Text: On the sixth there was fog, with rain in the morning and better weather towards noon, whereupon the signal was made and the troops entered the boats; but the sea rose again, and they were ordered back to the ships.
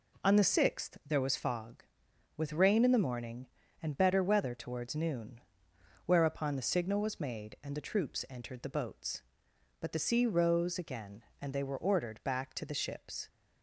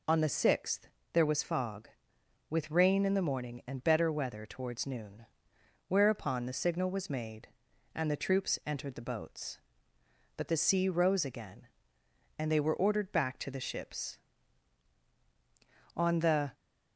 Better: first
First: none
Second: pauses between "sixth" and "there"; slight; at 0.8 s; 0.26 s long // goes on to say "On the"; from 15.9 s on; 0.56 s long

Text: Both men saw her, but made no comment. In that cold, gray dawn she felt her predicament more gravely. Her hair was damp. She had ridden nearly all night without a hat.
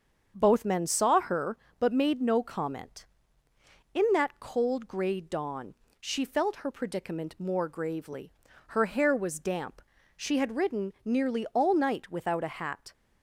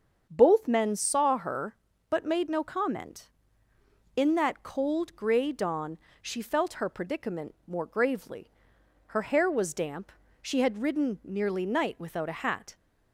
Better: first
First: starts louder than the rest; until 1.3 s; 6.5 dB // pauses between "dawn" and "she"; slight; at 5.7 s; 0.28 s long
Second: starts louder than the rest; until 1.3 s; 7 dB // pauses between "dawn" and "she"; slight; at 5.9 s; 0.24 s long // skips "all"; at 11.6 s

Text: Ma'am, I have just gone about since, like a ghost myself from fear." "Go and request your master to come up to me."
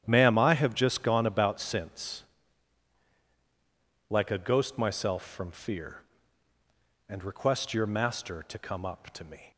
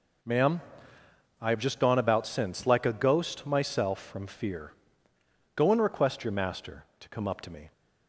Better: second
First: starts louder than the rest; strong; until 1.0 s; 10 dB // skips "Go"; at 6.5 s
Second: none

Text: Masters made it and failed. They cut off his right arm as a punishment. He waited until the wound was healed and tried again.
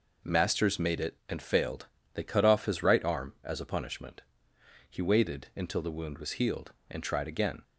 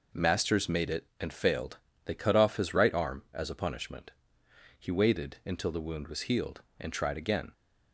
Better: neither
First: none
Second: none

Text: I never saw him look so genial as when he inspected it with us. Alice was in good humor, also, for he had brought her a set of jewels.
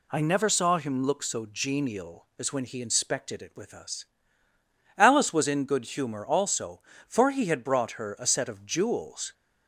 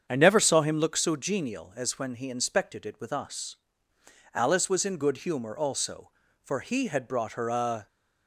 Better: first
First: none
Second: starts louder than the rest; strong; until 1.0 s; 7.5 dB // stops before "set of jewels"; at 7.8 s

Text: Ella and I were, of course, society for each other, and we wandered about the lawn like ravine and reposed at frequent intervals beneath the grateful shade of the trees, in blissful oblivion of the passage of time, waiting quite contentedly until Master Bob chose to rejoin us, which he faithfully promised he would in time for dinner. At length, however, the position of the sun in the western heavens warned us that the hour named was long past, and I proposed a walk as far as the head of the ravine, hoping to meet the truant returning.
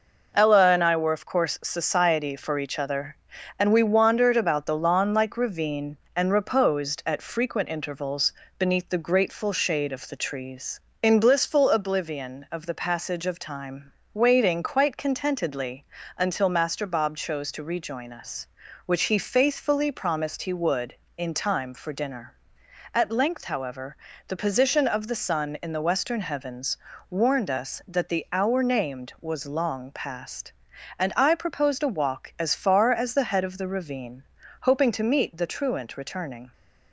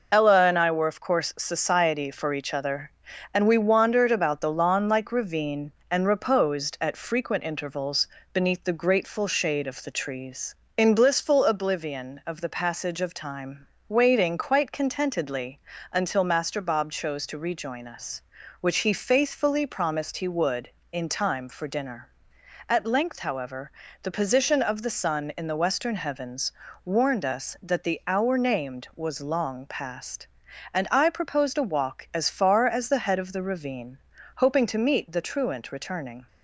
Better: first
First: pauses between "intervals" and "beneath"; slight; at 8.3 s; 0.26 s long // pauses between "contentedly" and "until"; slight; at 15.8 s; 0.34 s long // pauses between "heavens" and "warned"; slight; at 26.7 s; 0.34 s long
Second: loses the start of "Ella"; at 0.1 s; 35 ms // pauses between "intervals" and "beneath"; slight; at 8.0 s; 0.26 s long // pauses between "contentedly" and "until"; slight; at 15.5 s; 0.34 s long // pauses between "heavens" and "warned"; slight; at 26.5 s; 0.34 s long

